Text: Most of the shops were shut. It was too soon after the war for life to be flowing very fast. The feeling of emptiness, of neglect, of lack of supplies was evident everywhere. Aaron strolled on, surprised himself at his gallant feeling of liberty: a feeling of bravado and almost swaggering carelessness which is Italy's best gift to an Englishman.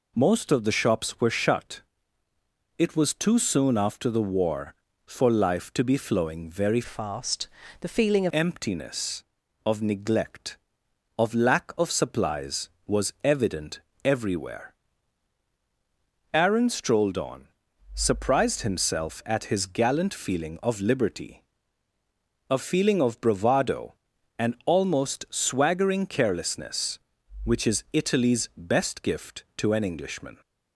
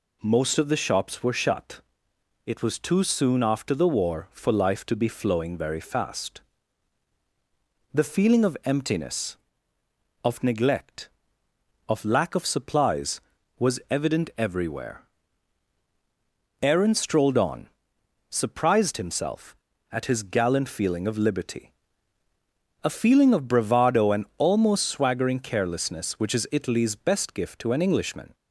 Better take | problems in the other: second | changes voice from "fast" to "of"; from 6.8 to 8.3 s; 1.5 s long // pauses between "evident" and "everywhere"; slight; at 13.7 s; 0.24 s long

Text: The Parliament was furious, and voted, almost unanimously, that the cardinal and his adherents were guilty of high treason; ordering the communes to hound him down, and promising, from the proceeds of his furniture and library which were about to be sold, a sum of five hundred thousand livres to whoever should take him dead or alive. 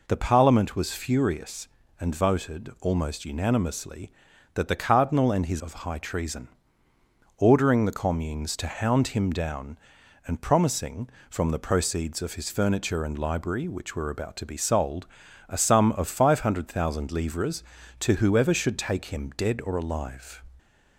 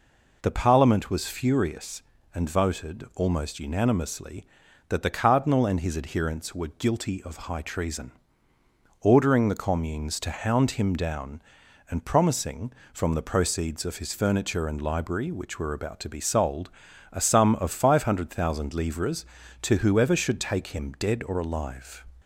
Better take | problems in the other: second | skips "adherents were guilty"; at 5.6 s // pauses between "of" and "high"; slight; at 5.7 s; 0.16 s long; slight in the second

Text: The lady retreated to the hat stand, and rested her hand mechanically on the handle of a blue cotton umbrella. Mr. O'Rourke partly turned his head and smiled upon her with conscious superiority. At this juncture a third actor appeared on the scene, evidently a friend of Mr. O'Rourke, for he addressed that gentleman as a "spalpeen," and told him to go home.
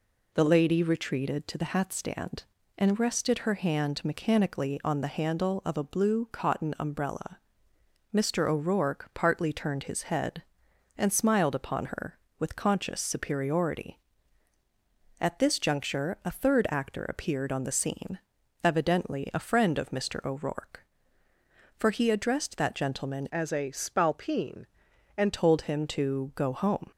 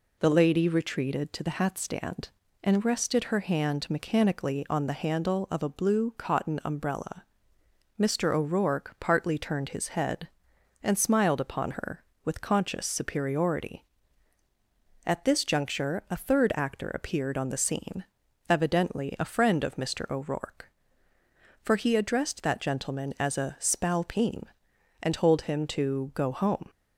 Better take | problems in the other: second | changes voice from "as" to "and"; from 23.3 to 25.3 s; 2.0 s long

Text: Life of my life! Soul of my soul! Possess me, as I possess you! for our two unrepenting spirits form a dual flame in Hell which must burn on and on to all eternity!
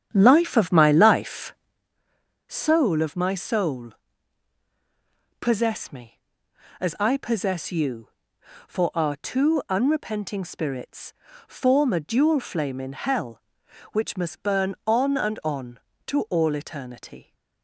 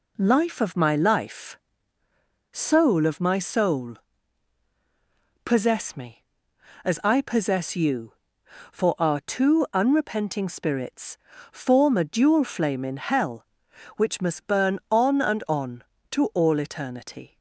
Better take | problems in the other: second | starts louder than the rest; strong; until 1.8 s; 9 dB // pauses between "spirits" and "form"; slight; at 11.1 s; 0.34 s long; slight in the second

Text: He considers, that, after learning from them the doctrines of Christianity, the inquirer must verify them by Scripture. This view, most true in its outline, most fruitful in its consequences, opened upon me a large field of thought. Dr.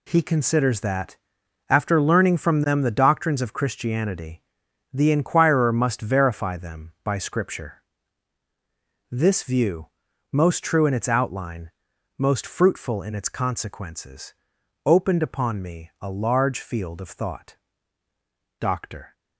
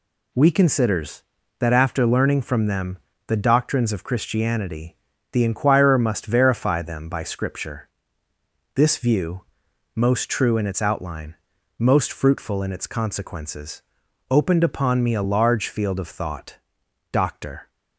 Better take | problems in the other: first | says "We" for "He"; at 0.3 s // pauses between "them" and "the"; slight; at 2.9 s; 0.28 s long

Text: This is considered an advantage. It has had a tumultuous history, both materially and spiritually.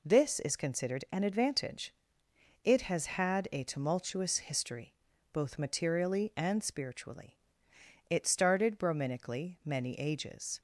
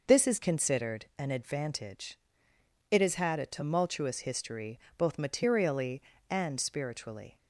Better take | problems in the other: second | goes on to say "It started Brahminically many ages"; strong; from 8.0 s on; 2.5 s long

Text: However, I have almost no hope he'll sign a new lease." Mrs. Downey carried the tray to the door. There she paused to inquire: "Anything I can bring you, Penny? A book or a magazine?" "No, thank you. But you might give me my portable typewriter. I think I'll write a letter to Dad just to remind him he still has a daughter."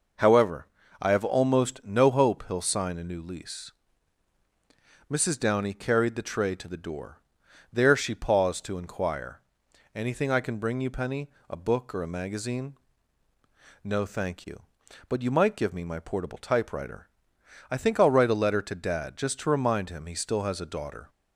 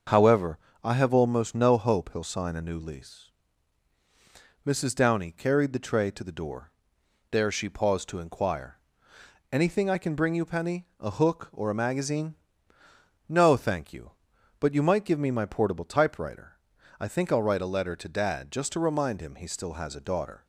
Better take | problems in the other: first | starts louder than the rest; until 1.3 s; 6.5 dB // says "hook" for "book"; at 11.1 s

